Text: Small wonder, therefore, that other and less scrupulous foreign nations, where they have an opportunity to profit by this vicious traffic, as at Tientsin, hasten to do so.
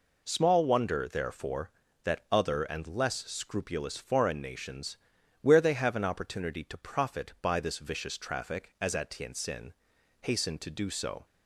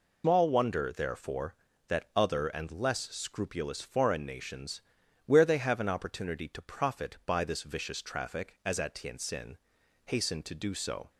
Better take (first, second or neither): first